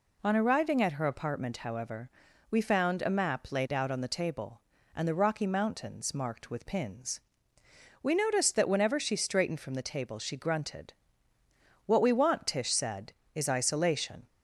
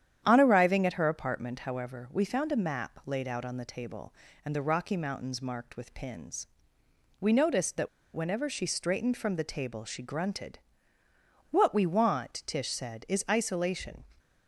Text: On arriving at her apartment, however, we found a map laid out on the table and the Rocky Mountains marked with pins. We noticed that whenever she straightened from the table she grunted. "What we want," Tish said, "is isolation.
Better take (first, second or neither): first